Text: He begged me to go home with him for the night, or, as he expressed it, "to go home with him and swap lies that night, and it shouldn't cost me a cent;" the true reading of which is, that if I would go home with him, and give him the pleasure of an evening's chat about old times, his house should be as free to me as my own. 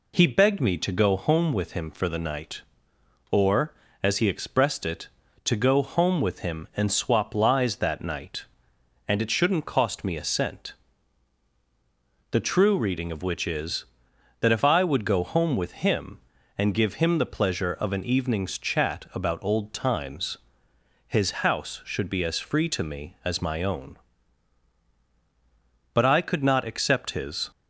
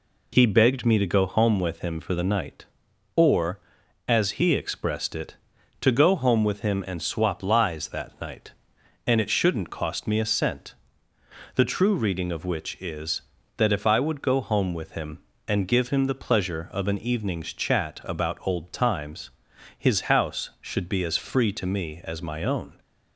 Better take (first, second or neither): second